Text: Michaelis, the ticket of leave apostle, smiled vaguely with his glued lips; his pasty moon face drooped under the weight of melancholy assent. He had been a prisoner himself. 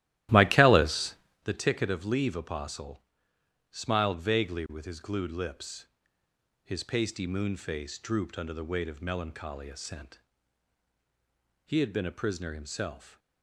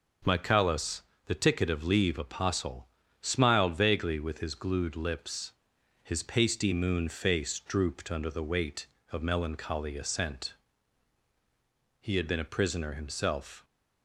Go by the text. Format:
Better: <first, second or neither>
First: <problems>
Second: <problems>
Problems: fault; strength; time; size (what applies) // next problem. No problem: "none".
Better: second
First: starts louder than the rest; strong; until 1.5 s; 14.5 dB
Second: none